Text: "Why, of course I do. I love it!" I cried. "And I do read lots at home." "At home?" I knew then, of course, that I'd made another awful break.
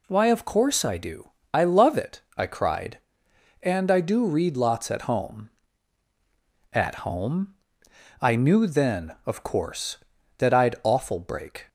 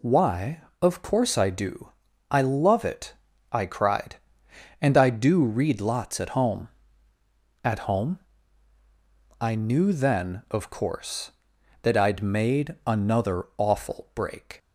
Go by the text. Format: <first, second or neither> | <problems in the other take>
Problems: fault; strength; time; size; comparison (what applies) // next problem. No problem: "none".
second | skips "made another"; at 10.7 s